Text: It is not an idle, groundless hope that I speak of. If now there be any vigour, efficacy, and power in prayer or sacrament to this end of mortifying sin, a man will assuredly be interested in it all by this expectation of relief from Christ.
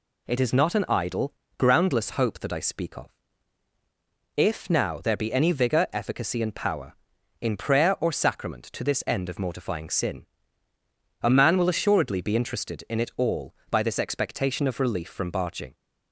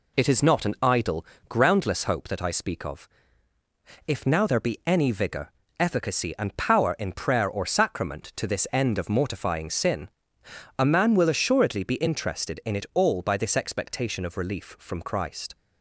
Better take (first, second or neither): second